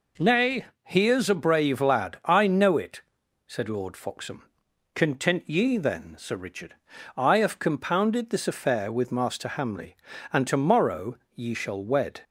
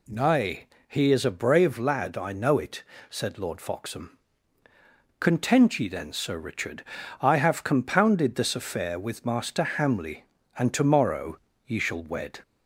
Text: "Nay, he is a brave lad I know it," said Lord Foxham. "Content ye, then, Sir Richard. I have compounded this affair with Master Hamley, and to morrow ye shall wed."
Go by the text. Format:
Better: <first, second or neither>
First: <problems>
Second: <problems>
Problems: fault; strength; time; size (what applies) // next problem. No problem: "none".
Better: neither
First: pauses between "morrow" and "ye"; slight; at 11.1 s; 0.16 s long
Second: pauses between "morrow" and "ye"; slight; at 11.3 s; 0.26 s long